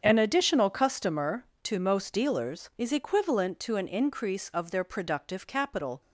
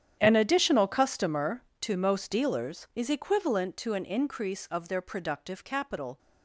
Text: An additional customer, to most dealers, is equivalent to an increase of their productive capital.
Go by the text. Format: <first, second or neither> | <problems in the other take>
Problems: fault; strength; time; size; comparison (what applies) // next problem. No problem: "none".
first | gets quieter; strong; throughout; 17 dB // starts louder than the rest; strong; until 1.2 s; 9.5 dB; strong in the first